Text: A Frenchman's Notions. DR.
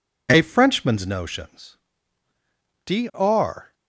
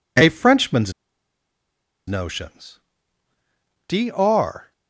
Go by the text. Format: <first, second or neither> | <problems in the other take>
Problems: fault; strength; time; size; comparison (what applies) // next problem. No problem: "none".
first | pauses between "Frenchman's" and "Notions"; at 0.9 s; 1.1 s long